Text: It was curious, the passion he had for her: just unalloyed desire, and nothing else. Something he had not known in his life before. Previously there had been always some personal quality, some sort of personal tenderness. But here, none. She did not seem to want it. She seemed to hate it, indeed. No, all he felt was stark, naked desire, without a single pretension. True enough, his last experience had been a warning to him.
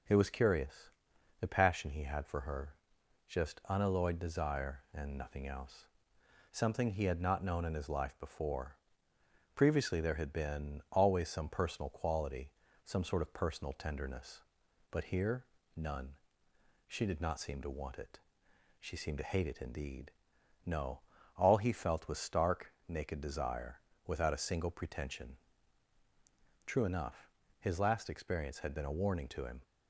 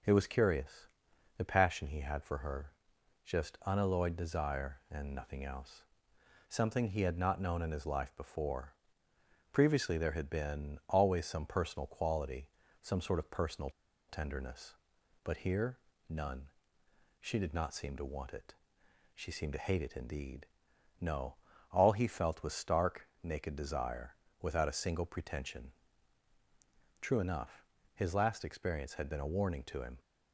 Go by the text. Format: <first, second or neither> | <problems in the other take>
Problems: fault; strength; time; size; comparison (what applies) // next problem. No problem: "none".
first | pauses between "personal" and "tenderness"; at 13.6 s; 0.38 s long